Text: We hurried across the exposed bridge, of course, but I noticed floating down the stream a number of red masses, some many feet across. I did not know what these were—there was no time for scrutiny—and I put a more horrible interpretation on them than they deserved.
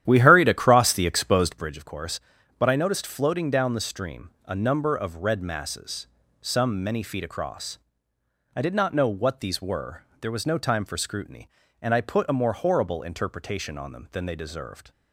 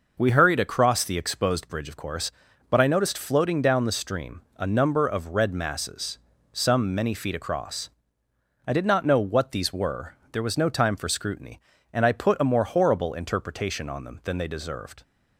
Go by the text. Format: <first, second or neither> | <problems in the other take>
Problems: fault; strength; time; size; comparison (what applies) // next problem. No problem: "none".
second | starts louder than the rest; strong; until 1.8 s; 11 dB // pauses between "stream" and "a"; slight; at 4.2 s; 0.16 s long; slight in the second